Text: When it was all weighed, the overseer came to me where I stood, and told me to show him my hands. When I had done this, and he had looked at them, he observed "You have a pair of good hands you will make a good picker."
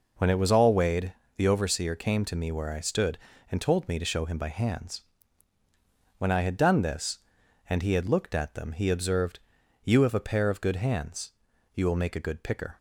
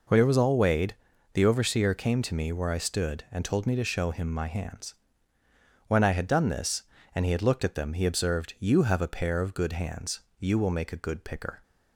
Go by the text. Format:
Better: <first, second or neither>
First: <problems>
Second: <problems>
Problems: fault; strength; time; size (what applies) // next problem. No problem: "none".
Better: second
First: says "by" for "my"; at 4.3 s // pauses between "observed" and "You"; at 9.3 s; 0.44 s long // pauses between "hands" and "you"; at 11.3 s; 0.44 s long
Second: pauses between "hands" and "you"; slight; at 10.2 s; 0.20 s long